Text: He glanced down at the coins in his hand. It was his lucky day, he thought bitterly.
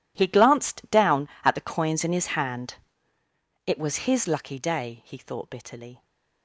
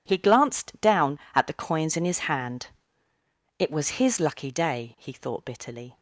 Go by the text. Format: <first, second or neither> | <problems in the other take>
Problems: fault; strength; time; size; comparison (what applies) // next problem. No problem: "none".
second | gets quieter; strong; throughout; 16 dB